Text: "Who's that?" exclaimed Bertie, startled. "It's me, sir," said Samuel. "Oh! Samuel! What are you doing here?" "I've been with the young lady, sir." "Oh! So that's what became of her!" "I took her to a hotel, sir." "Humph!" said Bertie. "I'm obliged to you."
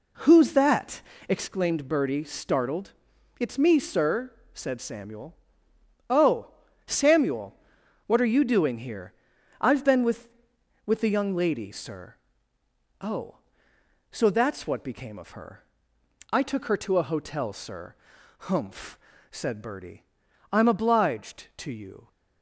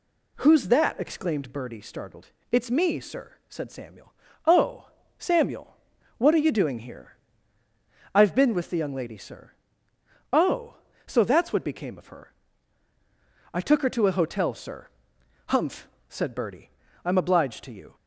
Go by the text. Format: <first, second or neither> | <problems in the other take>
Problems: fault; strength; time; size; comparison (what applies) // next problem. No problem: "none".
second | says "with" twice; at 10.8 s